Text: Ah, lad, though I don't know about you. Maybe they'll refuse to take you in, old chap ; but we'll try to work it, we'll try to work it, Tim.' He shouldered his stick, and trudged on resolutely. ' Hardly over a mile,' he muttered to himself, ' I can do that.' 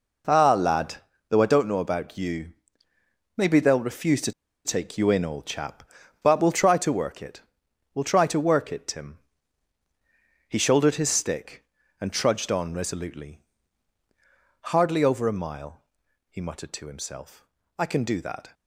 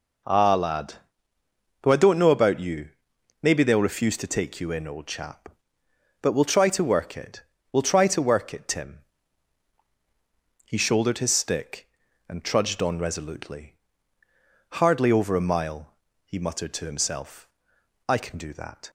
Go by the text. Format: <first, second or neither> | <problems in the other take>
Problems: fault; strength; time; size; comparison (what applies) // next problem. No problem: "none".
second | pauses between "to" and "take"; slight; at 4.3 s; 0.33 s long